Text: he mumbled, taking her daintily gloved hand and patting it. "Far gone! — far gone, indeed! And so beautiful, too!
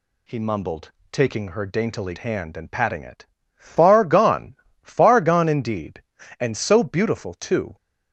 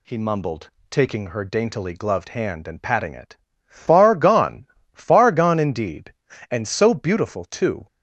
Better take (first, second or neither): second